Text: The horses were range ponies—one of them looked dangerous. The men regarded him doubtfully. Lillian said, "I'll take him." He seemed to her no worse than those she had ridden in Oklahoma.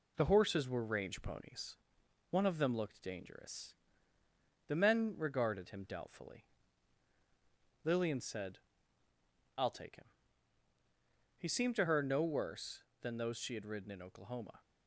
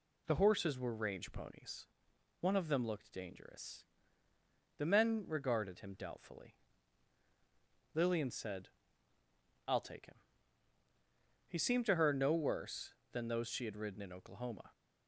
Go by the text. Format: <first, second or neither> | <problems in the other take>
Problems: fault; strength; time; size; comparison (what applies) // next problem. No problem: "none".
second | gets quieter; slight; throughout; 2 dB